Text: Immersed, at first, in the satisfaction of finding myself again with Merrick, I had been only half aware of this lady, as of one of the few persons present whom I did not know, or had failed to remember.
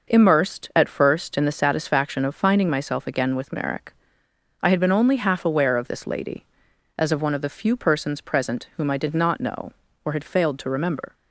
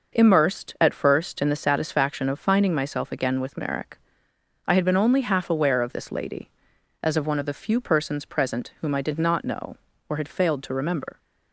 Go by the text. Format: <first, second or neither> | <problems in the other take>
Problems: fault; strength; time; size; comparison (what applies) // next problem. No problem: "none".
neither | none